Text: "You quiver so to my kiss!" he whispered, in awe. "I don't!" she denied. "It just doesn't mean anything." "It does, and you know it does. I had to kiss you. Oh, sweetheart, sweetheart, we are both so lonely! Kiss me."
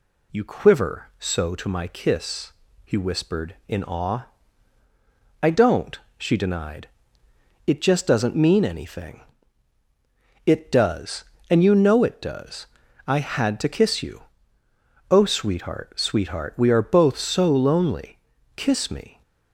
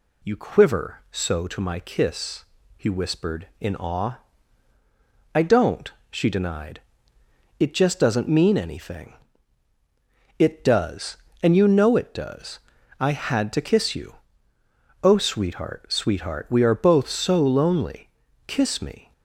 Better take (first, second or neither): neither